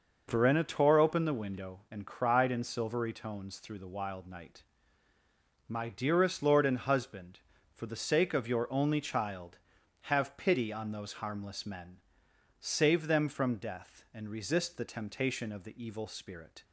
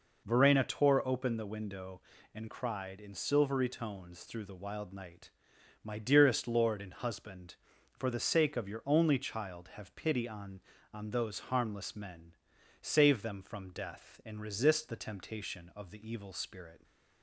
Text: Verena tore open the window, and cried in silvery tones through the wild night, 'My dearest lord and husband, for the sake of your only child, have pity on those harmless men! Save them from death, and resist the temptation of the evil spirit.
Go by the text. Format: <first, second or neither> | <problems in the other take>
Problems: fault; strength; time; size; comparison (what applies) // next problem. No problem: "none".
first | says "on" twice; at 10.9 s